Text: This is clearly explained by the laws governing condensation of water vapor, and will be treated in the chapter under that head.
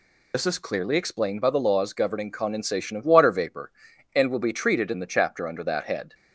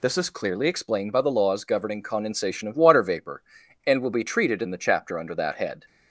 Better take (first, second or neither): second